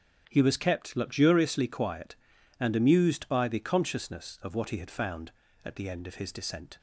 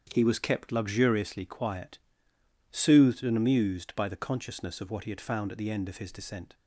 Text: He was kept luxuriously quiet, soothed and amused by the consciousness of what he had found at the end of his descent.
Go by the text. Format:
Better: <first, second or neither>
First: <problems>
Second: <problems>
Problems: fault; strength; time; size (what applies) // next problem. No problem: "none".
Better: second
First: starts louder than the rest; strong; until 1.2 s; 7.5 dB // skips "soothed"; at 2.3 s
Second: starts louder than the rest; strong; until 1.1 s; 8 dB